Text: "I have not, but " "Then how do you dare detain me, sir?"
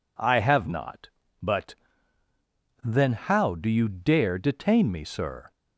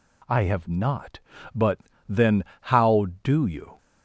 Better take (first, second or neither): first